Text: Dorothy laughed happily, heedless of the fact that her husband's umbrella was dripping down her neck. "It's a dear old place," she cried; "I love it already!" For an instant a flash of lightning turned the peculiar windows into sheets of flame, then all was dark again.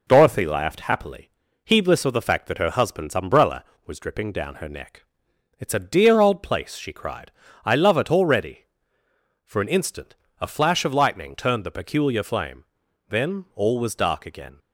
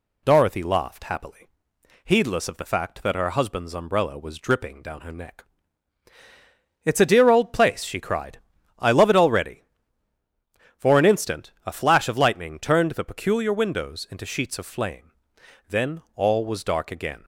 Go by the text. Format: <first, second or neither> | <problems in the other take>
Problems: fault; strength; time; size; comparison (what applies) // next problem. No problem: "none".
second | pauses between "instant" and "a"; slight; at 10.1 s; 0.26 s long // skips "windows into sheets of"; at 12.2 s